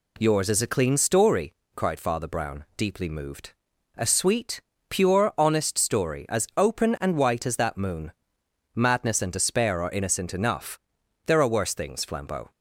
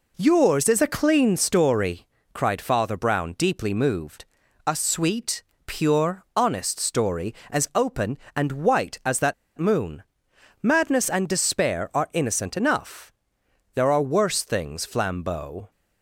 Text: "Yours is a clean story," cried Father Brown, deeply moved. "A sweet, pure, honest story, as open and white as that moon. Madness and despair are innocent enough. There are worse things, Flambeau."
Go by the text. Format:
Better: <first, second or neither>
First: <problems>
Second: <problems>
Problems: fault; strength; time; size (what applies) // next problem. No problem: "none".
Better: first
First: none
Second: pauses between "that" and "moon"; slight; at 9.3 s; 0.24 s long